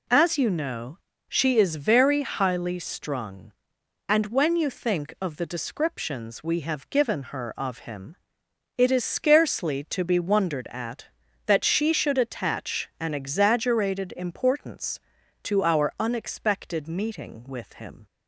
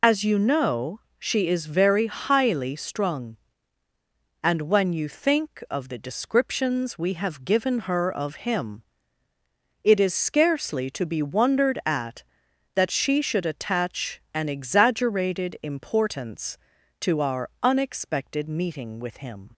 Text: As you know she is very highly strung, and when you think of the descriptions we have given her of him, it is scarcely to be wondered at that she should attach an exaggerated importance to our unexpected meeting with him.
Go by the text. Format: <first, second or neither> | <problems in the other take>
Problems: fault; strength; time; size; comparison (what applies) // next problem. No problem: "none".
first | loses the start of "As"; at 0.0 s; 60 ms // pauses between "know" and "she"; slight; at 0.9 s; 0.24 s long; slight in the first